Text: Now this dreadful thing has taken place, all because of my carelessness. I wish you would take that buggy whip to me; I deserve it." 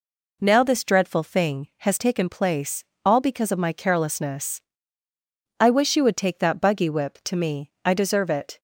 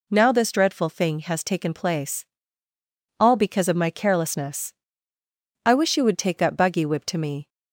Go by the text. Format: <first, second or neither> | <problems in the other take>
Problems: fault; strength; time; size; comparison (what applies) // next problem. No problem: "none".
first | stops before "I deserve it"; at 7.4 s